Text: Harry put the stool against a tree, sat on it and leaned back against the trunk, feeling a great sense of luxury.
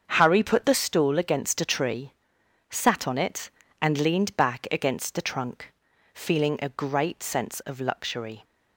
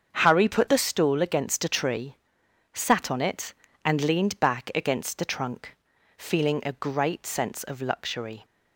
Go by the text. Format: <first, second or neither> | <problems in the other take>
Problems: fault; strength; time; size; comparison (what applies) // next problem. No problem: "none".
neither | starts louder than the rest; the same in both